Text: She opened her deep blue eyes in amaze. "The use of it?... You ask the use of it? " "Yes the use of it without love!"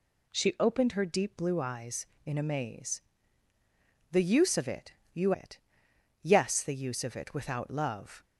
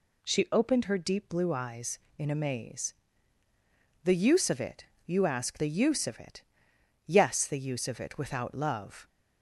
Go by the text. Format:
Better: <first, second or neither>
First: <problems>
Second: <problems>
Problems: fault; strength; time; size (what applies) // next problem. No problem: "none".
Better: second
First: skips "ask the use of"; at 5.3 s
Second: none